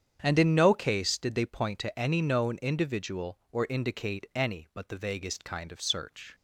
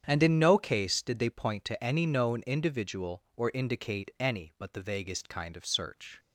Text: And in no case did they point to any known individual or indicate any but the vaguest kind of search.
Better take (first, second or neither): neither